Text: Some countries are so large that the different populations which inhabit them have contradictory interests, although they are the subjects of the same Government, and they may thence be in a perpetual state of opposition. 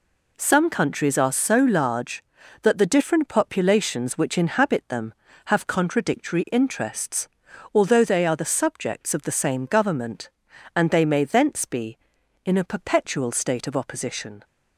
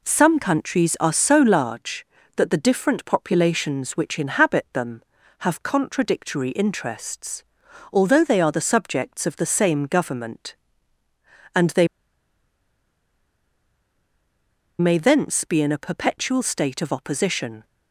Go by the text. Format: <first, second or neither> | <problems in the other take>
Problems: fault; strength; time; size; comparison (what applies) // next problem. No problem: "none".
first | pauses between "they" and "may"; strong; at 11.8 s; 2.9 s long